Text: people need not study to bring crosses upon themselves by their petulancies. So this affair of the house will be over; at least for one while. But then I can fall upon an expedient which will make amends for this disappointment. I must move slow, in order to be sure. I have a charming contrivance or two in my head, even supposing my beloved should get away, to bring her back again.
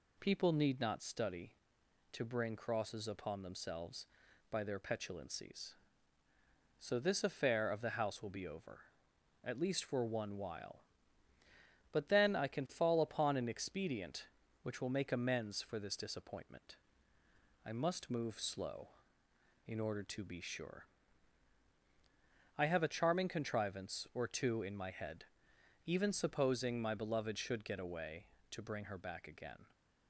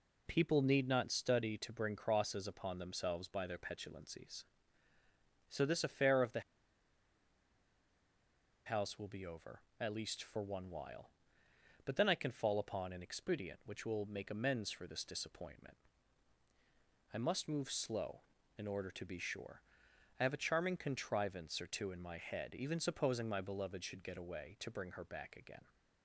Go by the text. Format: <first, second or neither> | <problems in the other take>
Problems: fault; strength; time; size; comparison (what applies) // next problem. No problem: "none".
first | pauses between "the" and "house"; strong; at 6.4 s; 2.2 s long